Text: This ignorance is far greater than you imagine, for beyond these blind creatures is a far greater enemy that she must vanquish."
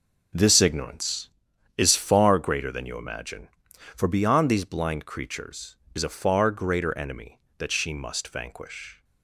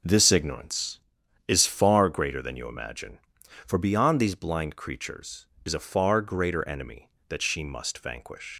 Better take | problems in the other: first | leaves "vanquish" unfinished; at 8.5 s; 155 ms

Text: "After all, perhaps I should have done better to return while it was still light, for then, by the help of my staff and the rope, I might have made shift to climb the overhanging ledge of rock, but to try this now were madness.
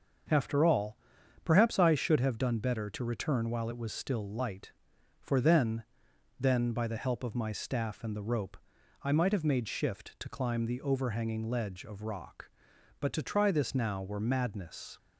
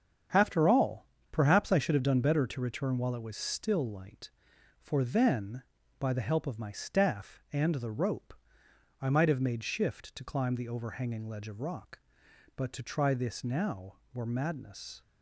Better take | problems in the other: second | starts louder than the rest; until 1.7 s; 6.5 dB; strong in the second // says "then" twice; at 6.3 s

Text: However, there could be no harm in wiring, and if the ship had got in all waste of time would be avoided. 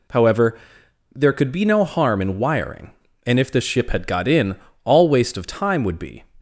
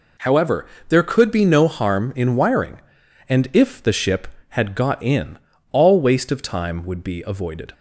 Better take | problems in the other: second | pauses between "in" and "all"; slight; at 4.5 s; 0.30 s long; slight in the second // stops before "avoided"; at 6.3 s

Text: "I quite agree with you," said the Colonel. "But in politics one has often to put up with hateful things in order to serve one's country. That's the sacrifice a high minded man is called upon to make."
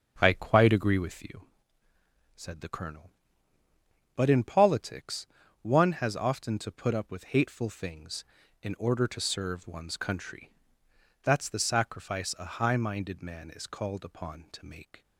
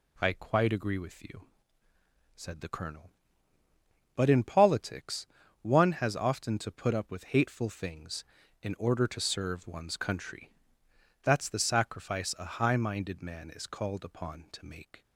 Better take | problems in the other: second | starts louder than the rest; until 1.3 s; 7 dB // pauses between "politics" and "one"; slight; at 5.2 s; 0.34 s long; slight in the second

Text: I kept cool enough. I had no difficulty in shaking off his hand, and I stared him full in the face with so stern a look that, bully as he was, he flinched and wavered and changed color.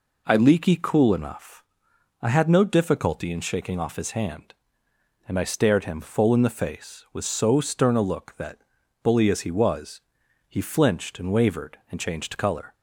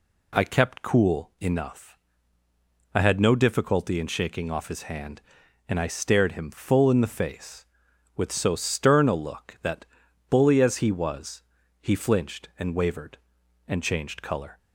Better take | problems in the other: second | says "leaky" for "kept"; at 0.3 s

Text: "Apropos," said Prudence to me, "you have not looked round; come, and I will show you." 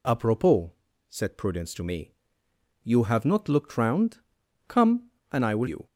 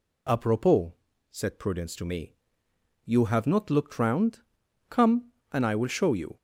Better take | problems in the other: second | skips "show"; at 5.6 s

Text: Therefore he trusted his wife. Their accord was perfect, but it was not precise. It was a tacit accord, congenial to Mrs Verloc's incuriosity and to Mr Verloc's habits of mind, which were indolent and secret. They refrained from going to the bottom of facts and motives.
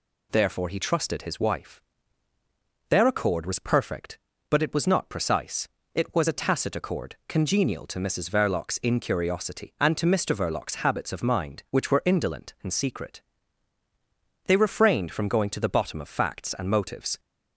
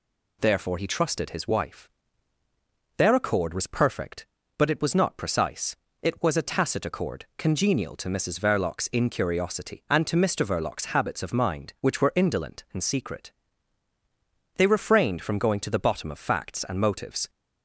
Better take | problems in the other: neither | none

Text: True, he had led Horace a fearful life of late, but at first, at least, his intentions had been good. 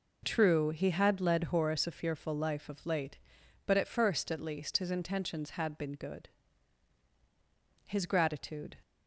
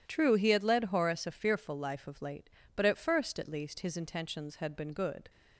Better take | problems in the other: second | goes on to say "His gratitude"; noticeable; from 7.8 s on; 0.92 s long

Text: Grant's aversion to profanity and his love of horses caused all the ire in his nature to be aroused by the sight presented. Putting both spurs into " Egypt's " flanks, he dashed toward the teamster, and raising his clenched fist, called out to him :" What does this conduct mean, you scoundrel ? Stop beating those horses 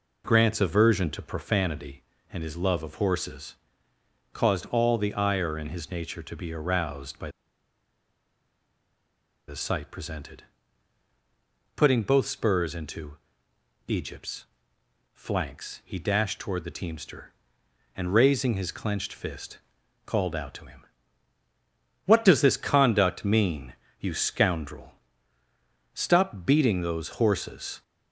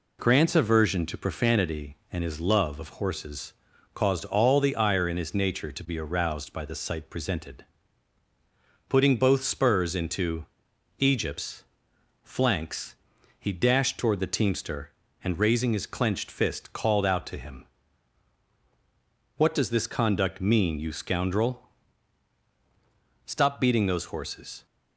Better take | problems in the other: second | pauses between "horses" and "caused"; noticeable; at 3.5 s; 0.80 s long; also in the second // pauses between "by" and "the"; strong; at 7.2 s; 2.1 s long

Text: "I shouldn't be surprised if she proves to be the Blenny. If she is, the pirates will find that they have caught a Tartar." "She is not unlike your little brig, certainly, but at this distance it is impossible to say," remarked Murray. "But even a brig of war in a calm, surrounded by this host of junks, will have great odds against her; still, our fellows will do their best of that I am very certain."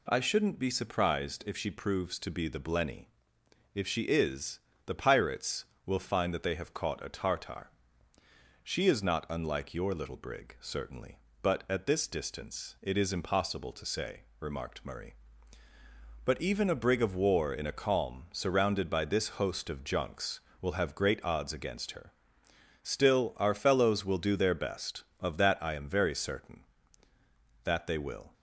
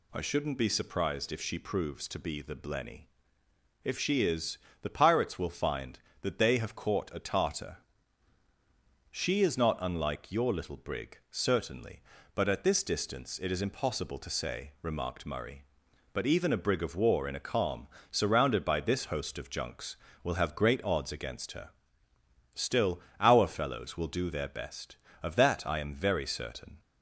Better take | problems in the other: second | goes on to say "That they will"; noticeable; from 27.6 s on; 0.68 s long

